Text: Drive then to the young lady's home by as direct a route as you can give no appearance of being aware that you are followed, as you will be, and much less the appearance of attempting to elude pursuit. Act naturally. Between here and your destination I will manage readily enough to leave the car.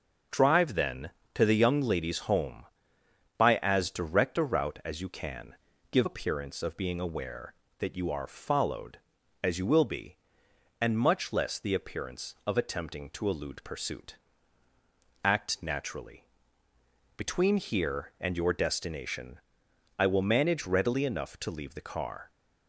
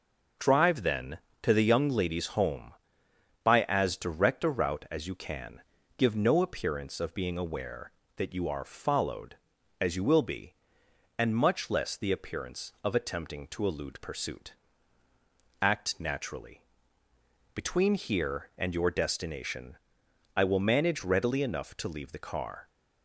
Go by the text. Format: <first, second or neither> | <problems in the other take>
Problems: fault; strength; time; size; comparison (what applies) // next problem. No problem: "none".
second | starts louder than the rest; until 1.5 s; 6.5 dB // pauses between "can" and "give"; slight; at 5.5 s; 0.36 s long; slight in the second // skips "no"; at 6.0 s // pauses between "destination" and "I"; noticeable; at 19.3 s; 0.58 s long; noticeable in the second